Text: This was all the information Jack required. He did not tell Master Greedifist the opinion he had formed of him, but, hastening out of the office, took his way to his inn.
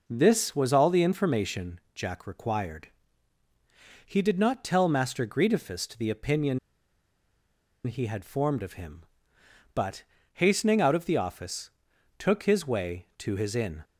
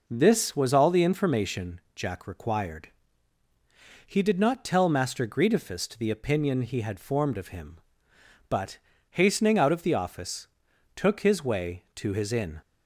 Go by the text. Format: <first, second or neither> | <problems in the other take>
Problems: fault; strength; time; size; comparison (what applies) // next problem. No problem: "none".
second | pauses between "information" and "Jack"; slight; at 1.7 s; 0.16 s long; slight in the second // pauses between "opinion" and "he"; strong; at 6.5 s; 1.2 s long